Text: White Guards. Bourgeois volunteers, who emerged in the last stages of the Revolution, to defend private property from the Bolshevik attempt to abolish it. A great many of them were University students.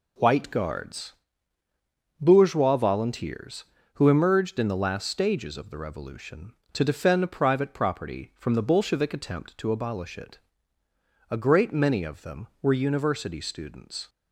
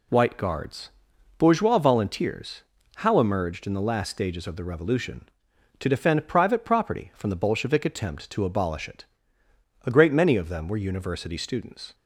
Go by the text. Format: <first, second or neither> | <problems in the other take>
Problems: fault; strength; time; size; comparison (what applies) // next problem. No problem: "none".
first | says "how" for "who"; at 2.9 s